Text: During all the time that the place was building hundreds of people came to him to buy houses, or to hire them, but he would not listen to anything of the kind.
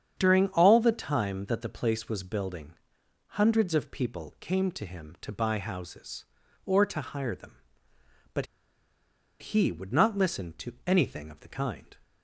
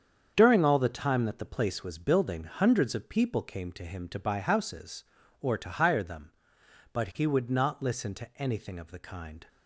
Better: second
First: starts louder than the rest; strong; until 1.1 s; 8 dB // pauses between "building" and "hundreds"; noticeable; at 2.7 s; 0.60 s long // pauses between "but" and "he"; noticeable; at 8.4 s; 0.94 s long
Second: starts louder than the rest; strong; until 1.3 s; 7.5 dB

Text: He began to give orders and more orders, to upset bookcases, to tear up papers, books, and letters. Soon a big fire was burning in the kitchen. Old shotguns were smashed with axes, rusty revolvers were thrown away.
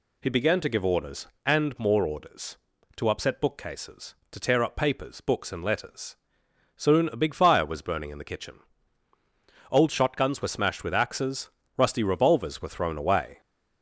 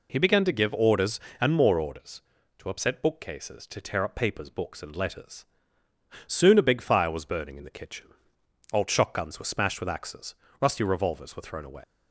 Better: first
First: none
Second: leaves "away" unfinished; at 11.8 s; 130 ms

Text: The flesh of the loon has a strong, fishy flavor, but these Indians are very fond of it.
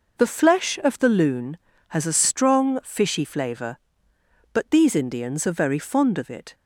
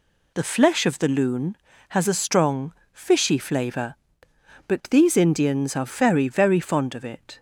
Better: first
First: none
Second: says "very" twice; at 6.2 s

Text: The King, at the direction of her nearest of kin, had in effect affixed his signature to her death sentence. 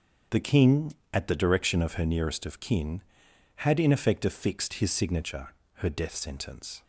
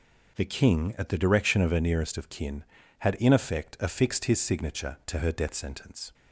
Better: second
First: starts louder than the rest; strong; until 1.5 s; 7.5 dB // skips "to"; at 5.6 s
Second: none

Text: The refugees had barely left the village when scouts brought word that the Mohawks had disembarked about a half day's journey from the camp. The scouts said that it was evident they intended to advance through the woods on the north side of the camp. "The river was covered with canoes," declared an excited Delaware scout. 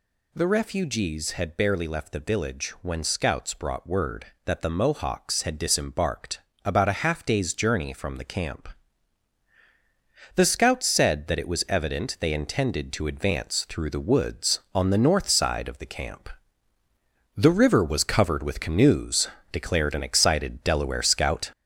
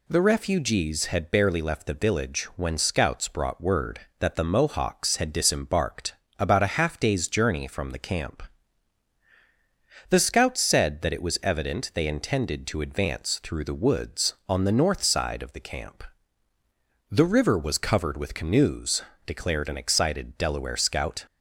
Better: second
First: gets louder; noticeable; throughout; 4.5 dB // pauses between "disembarked" and "about"; slight; at 6.3 s; 0.26 s long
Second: pauses between "disembarked" and "about"; slight; at 6.1 s; 0.26 s long

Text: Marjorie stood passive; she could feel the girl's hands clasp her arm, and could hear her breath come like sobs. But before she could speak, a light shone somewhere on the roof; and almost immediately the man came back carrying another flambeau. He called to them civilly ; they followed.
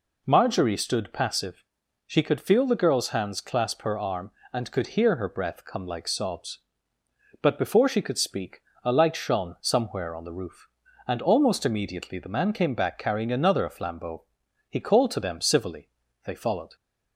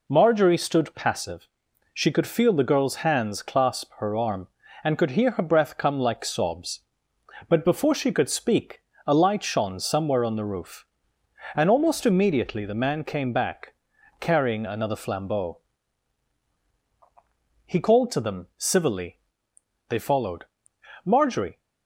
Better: first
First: none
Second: pauses between "back" and "carrying"; at 13.7 s; 0.44 s long // goes on to say "Marjorie"; from 21.0 s on; 0.54 s long

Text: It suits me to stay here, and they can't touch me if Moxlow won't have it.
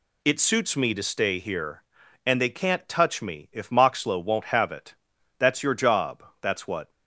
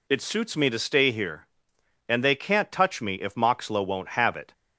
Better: second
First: goes on to say "That's your job that's what"; from 5.3 s on; 1.5 s long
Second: none

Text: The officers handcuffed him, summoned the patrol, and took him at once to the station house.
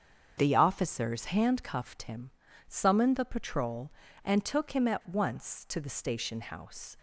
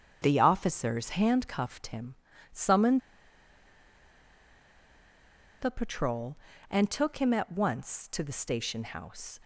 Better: first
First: starts louder than the rest; strong; until 1.3 s; 7.5 dB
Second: starts louder than the rest; strong; until 1.2 s; 7.5 dB // pauses between "summoned" and "the"; strong; at 3.0 s; 2.6 s long

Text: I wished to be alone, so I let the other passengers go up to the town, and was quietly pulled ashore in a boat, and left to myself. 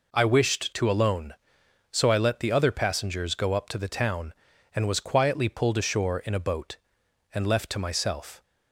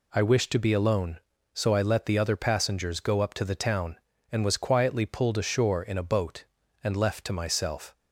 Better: second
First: skips "be"; at 0.9 s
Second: none

